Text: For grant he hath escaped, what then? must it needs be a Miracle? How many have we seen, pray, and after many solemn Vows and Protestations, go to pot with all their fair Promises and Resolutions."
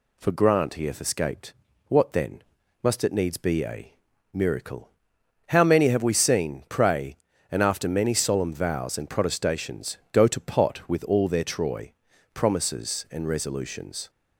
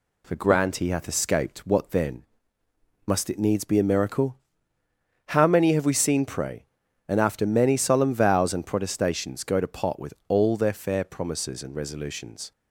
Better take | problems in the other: second | pauses between "a" and "Miracle"; at 3.9 s; 0.42 s long // says "troy" for "fair"; at 11.4 s

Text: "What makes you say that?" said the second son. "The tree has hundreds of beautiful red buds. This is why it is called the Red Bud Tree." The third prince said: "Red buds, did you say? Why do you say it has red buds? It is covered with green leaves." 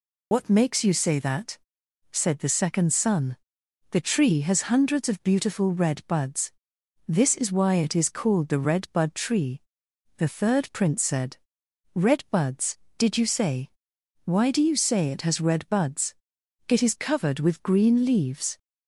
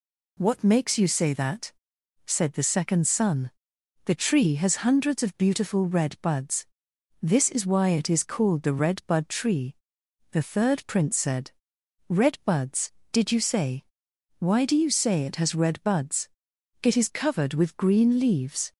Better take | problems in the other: second | loses the start of "What"; at 0.3 s; 75 ms

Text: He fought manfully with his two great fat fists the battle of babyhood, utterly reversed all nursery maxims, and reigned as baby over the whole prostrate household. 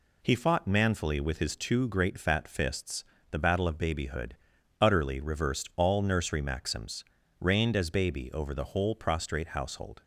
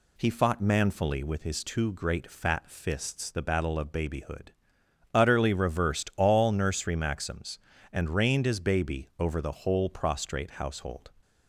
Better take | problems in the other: second | pauses between "fists" and "the"; slight; at 3.0 s; 0.28 s long // skips "and"; at 7.2 s

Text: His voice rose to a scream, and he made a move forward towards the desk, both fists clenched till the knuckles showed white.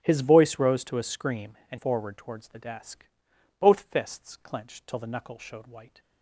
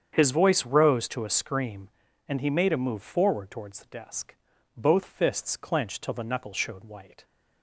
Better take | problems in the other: second | starts louder than the rest; strong; until 1.0 s; 13.5 dB; strong in the second // skips "he made a move"; at 1.7 s

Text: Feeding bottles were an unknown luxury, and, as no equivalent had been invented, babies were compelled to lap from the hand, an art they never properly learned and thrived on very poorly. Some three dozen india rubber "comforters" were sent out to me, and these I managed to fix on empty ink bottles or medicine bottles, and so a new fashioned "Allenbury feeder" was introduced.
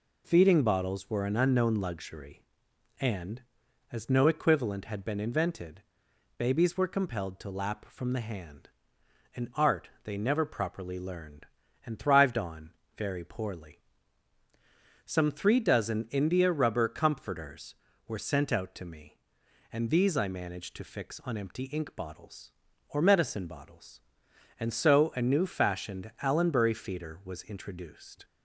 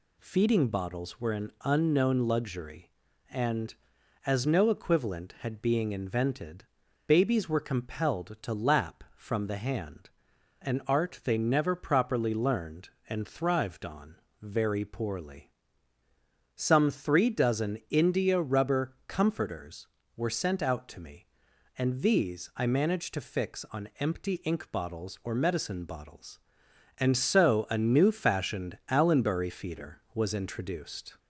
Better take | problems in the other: first | says "being" for "been"; at 5.6 s // pauses between "on" and "very"; slight; at 14.1 s; 0.26 s long; slight in the first

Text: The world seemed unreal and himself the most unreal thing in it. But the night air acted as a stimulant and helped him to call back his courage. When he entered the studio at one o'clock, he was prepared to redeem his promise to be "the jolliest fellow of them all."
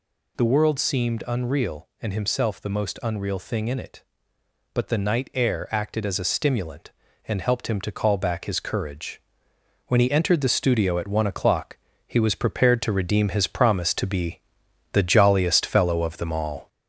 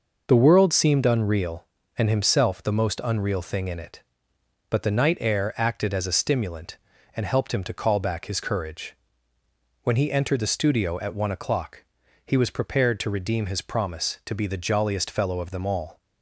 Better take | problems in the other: second | gets louder; slight; throughout; 3 dB // pauses between "be" and "the"; noticeable; at 14.3 s; 0.52 s long

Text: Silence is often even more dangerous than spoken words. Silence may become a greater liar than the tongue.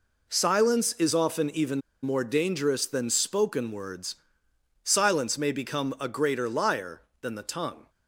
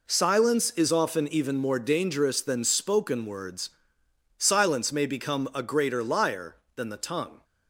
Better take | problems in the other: second | pauses between "even" and "more"; slight; at 1.7 s; 0.23 s long

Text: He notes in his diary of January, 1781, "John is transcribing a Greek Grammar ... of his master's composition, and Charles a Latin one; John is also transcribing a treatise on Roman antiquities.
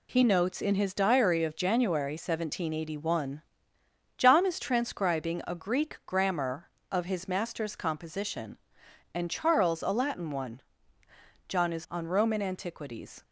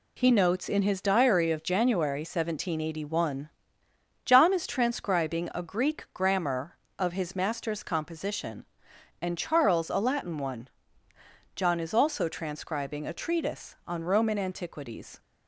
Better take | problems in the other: second | skips "also transcribing a treatise"; at 11.8 s

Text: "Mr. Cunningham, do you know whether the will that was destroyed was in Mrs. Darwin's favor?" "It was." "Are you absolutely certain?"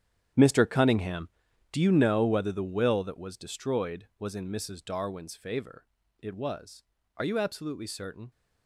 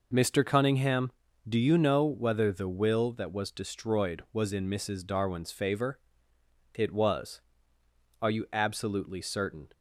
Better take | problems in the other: second | gets quieter; strong; throughout; 15 dB

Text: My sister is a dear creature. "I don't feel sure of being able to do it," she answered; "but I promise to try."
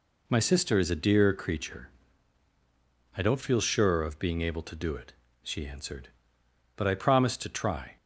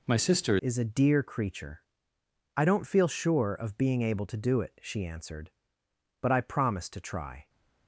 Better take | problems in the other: first | changes voice at "is"; from 0.5 s on; 6.9 s long

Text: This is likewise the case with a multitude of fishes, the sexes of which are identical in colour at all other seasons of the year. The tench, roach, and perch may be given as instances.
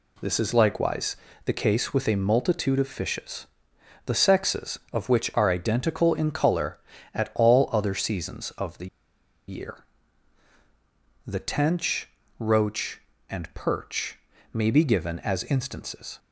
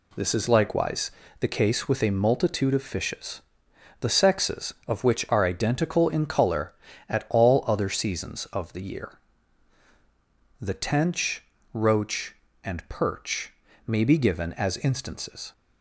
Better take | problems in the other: second | pauses between "likewise" and "the"; slight; at 1.1 s; 0.30 s long; slight in the second // pauses between "the" and "year"; noticeable; at 8.8 s; 0.60 s long // pauses between "perch" and "may"; slight; at 14.1 s; 0.34 s long; slight in the second

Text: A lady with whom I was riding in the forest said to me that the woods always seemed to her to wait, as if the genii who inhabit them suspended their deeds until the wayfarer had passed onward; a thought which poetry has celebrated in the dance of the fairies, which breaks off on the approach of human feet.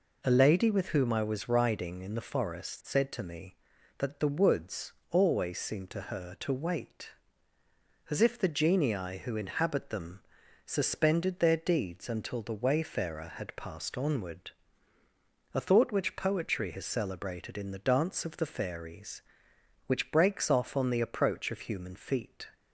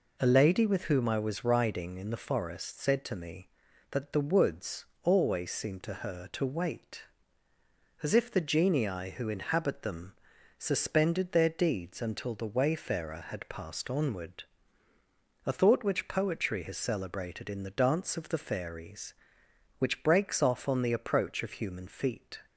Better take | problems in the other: neither | pauses between "woods" and "always"; slight; the same in both // pauses between "them" and "suspended"; the same in both

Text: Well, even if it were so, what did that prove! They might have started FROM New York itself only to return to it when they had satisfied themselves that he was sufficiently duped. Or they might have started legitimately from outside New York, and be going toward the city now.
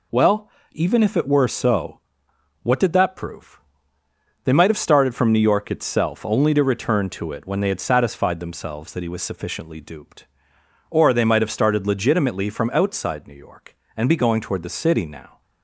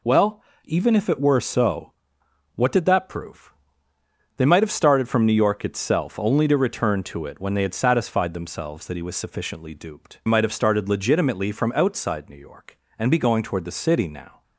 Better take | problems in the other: first | skips "Or they"; at 10.2 s

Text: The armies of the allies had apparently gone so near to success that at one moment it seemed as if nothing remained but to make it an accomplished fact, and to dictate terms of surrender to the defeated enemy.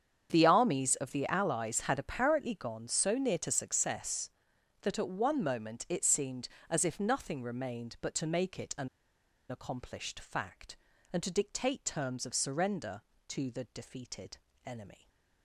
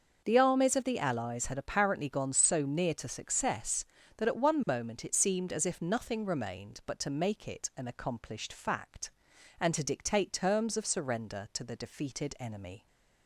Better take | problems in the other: second | starts louder than the rest; strong; until 1.3 s; 8 dB; noticeable in the second // pauses between "an" and "accomplished"; noticeable; at 8.8 s; 0.61 s long // pauses between "defeated" and "enemy"; slight; at 14.3 s; 0.30 s long // stays silent after the last word; slight; from 14.9 s on; 0.5 s long

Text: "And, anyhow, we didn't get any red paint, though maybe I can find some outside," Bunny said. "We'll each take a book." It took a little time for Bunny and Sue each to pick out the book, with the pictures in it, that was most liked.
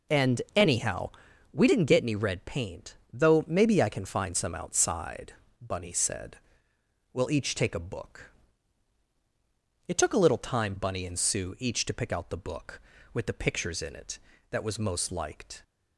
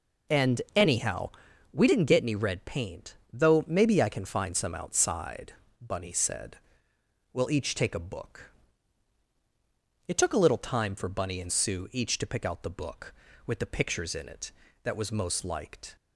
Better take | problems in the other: second | skips "for"; at 10.7 s

